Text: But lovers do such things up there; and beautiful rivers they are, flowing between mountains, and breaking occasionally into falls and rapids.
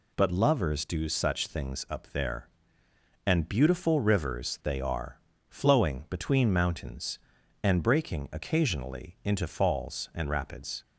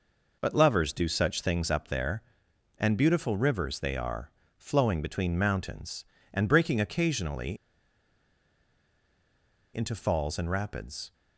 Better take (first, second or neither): first